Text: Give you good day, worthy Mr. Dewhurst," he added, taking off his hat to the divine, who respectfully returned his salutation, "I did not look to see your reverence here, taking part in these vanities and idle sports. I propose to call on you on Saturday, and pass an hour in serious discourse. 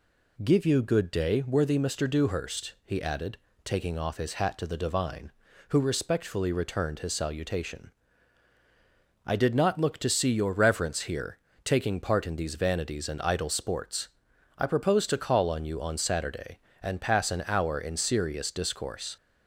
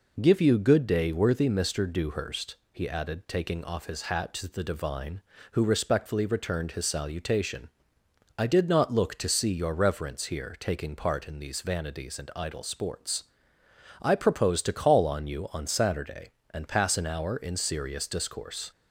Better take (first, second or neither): neither